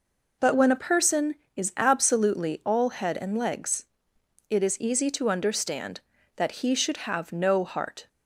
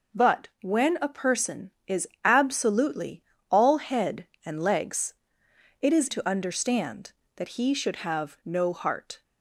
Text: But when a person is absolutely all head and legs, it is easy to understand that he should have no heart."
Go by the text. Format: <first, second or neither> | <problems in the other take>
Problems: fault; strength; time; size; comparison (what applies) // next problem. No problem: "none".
first | pauses between "is" and "absolutely"; slight; at 2.0 s; 0.18 s long // pauses between "absolutely" and "all"; slight; at 3.2 s; 0.30 s long // skips "easy"; at 6.0 s